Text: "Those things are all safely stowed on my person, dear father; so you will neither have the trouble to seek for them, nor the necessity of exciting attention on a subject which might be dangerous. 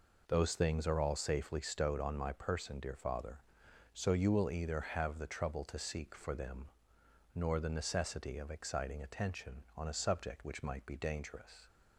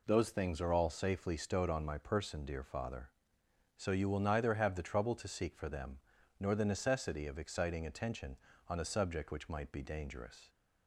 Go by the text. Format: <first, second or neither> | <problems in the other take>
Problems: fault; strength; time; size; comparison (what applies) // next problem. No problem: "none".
second | says "either" for "neither"; at 4.4 s